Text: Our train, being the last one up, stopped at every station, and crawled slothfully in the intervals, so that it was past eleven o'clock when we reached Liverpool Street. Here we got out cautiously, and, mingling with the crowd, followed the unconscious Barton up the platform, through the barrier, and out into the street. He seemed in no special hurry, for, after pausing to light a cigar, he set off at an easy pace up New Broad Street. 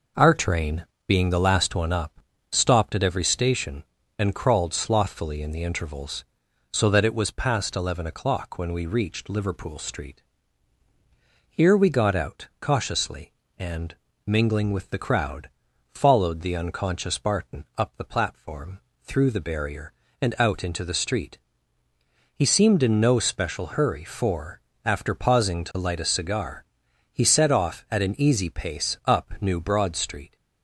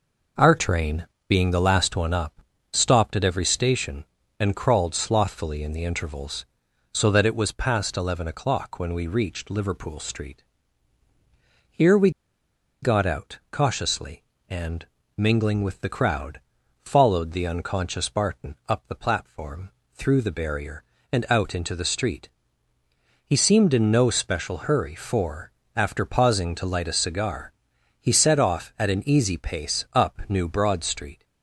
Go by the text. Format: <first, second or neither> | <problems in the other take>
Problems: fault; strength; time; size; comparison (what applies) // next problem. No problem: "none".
first | pauses between "we" and "got"; noticeable; at 12.0 s; 0.72 s long